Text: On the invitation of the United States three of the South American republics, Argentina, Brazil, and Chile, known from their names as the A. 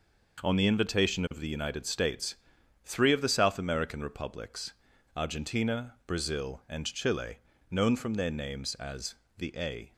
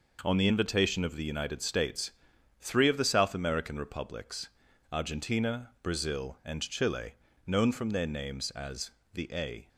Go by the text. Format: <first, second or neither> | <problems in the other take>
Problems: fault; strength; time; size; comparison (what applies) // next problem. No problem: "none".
neither | pauses between "States" and "three"; noticeable; the same in both // pauses between "as" and "the"; slight; the same in both